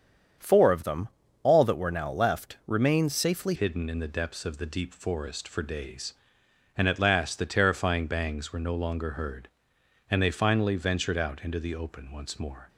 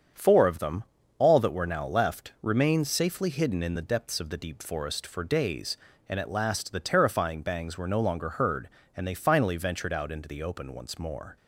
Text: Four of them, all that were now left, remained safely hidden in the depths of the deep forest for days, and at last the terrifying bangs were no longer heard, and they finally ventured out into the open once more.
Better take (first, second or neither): second